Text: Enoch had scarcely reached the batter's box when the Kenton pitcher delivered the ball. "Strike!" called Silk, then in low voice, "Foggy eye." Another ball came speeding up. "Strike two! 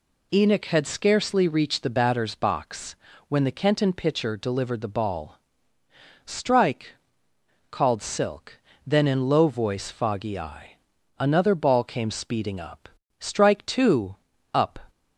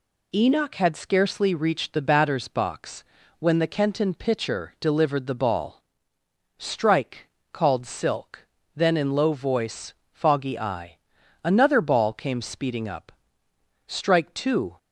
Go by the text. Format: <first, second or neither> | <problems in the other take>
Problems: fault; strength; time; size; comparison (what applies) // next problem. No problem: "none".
second | pauses between "box" and "when"; slight; at 2.9 s; 0.34 s long; slight in the second // goes on to say "up"; slight; from 14.5 s on; 0.24 s long